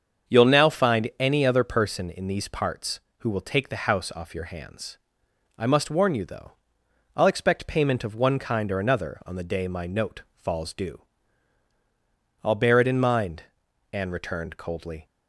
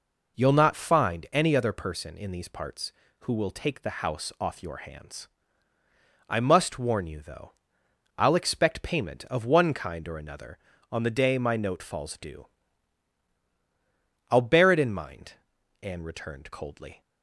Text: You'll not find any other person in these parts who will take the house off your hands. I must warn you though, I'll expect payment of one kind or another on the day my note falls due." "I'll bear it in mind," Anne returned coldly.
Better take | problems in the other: second | starts louder than the rest; strong; until 1.4 s; 7 dB // says "now" for "not"; at 0.4 s

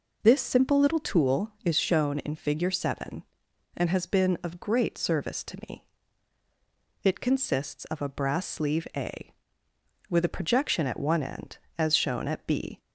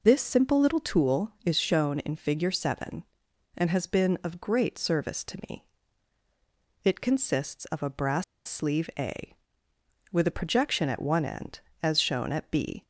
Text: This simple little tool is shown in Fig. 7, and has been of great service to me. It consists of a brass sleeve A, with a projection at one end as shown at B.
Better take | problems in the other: first | pauses between "brass" and "sleeve"; slight; at 8.2 s; 0.24 s long

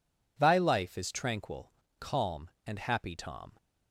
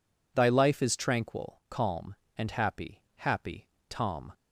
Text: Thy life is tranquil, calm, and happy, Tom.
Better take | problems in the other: first | says "happy" twice; at 3.1 s

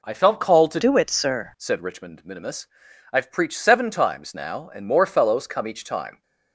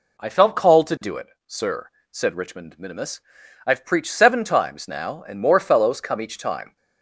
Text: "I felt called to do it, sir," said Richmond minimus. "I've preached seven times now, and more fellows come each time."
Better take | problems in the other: second | changes voice from "do" to "sir"; from 0.8 to 1.5 s; 0.7 s long

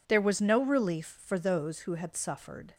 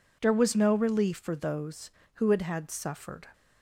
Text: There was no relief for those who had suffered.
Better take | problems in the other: first | says "had" twice; at 2.4 s

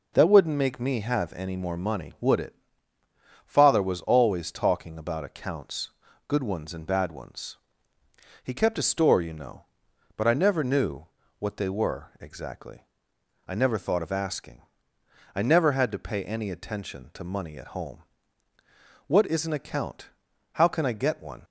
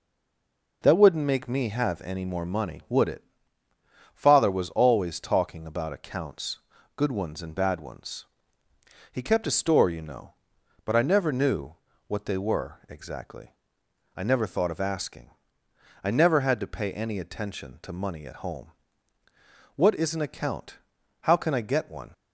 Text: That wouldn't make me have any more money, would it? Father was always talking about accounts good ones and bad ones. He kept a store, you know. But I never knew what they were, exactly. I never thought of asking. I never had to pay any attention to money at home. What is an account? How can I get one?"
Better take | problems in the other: first | stays silent before the first word; slight; until 0.8 s; 0.8 s long // pauses between "accounts" and "good"; slight; at 6.5 s; 0.36 s long; slight in the first // pauses between "knew" and "what"; slight; at 11.7 s; 0.34 s long; slight in the first

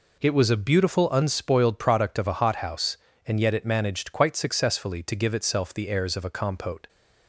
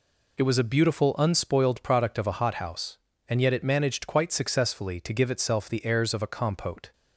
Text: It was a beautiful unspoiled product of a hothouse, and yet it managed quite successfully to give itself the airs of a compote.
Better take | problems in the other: neither | none

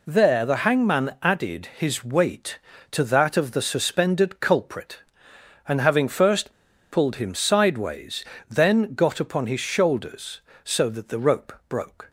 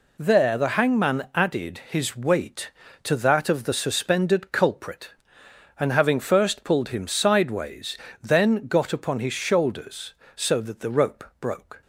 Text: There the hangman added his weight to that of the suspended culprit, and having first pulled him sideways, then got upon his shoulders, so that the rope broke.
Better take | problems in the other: second | pauses between "first" and "pulled"; at 6.5 s; 0.40 s long // pauses between "rope" and "broke"; slight; at 11.5 s; 0.16 s long; slight in the second

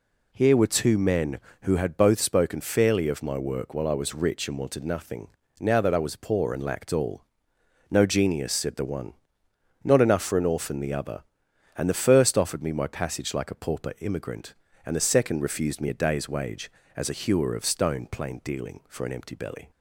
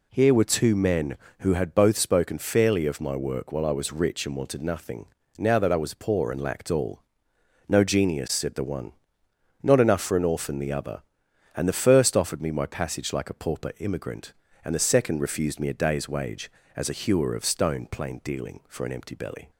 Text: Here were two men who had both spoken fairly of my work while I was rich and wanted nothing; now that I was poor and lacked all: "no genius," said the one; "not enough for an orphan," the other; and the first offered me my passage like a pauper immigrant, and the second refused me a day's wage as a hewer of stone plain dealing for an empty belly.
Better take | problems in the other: neither | none

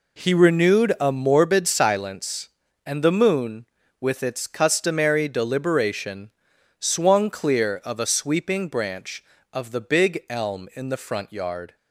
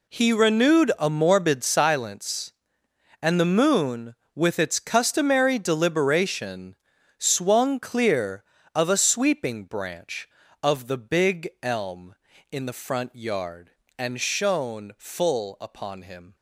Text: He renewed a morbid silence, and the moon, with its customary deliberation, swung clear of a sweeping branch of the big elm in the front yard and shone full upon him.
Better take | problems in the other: second | stops before "and shone full upon him"; at 11.7 s

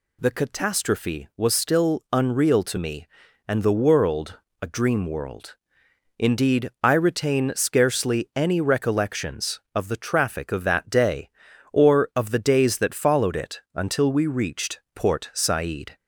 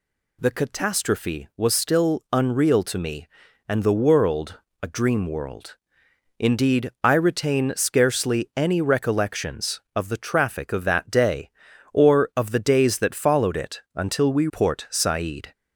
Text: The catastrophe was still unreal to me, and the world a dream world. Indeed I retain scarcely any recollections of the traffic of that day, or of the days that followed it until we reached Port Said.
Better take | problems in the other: first | pauses between "world" and "a"; slight; at 4.5 s; 0.24 s long; slight in the first // skips "reached"; at 14.4 s

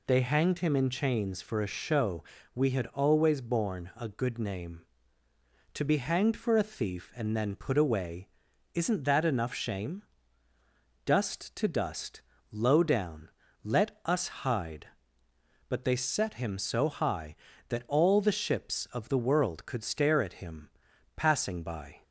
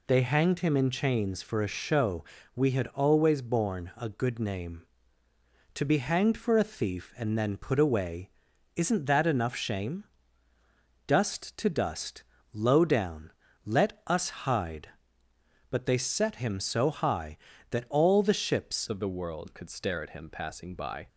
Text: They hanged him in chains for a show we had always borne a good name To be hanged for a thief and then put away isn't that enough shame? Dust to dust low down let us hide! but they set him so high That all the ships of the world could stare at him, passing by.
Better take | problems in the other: first | pauses between "show" and "we"; slight; at 2.2 s; 0.30 s long; slight in the first // pauses between "away" and "isn't"; noticeable; at 8.3 s; 0.46 s long; noticeable in the first // pauses between "dust" and "low"; slight; at 12.2 s; 0.30 s long; slight in the first // pauses between "down" and "let"; slight; at 13.3 s; 0.34 s long; slight in the first // changes voice at "of"; from 18.8 s on; 2.2 s long

